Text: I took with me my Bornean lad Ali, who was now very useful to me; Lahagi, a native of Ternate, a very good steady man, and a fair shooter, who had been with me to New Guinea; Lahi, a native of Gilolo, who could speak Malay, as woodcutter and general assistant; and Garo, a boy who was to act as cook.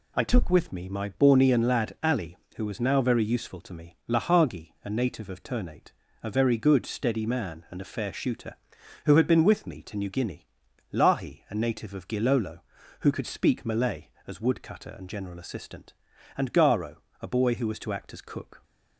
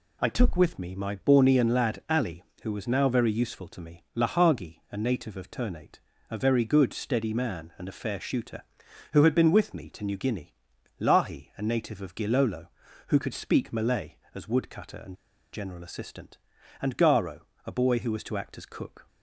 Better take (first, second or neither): first